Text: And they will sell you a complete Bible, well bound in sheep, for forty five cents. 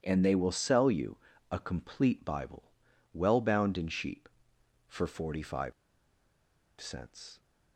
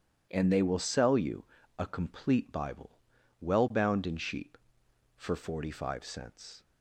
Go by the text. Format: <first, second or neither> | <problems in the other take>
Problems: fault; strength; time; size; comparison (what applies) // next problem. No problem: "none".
second | pauses between "you" and "a"; slight; at 1.1 s; 0.34 s long; slight in the second // pauses between "five" and "cents"; at 5.7 s; 1.0 s long